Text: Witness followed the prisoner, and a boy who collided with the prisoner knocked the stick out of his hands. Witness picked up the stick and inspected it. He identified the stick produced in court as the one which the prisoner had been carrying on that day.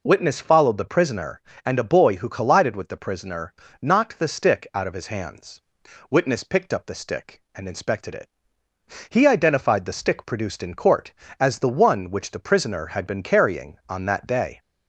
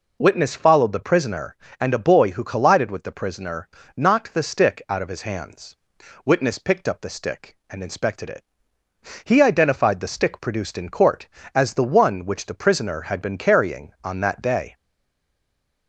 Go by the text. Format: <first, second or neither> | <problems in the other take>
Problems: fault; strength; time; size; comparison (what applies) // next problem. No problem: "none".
first | pauses between "prisoner" and "knocked"; slight; at 3.6 s; 0.28 s long; slight in the first // stays silent after the last word; from 14.7 s on; 1.1 s long